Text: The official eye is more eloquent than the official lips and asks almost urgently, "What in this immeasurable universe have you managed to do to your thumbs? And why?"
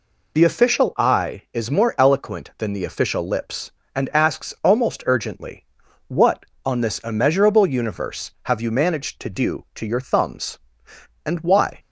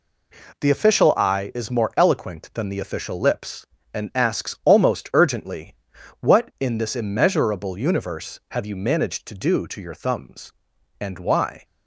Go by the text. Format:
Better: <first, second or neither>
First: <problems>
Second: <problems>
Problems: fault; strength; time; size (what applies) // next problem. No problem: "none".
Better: second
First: says "on" for "in"; at 6.6 s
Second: none